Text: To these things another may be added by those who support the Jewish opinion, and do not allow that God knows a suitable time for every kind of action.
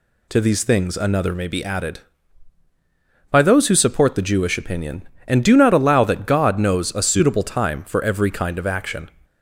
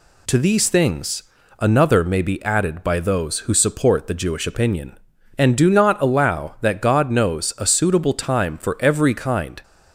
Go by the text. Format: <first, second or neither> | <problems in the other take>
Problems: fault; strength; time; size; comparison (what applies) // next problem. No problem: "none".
first | pauses between "things" and "another"; slight; at 1.2 s; 0.36 s long // stops before "of action"; at 9.6 s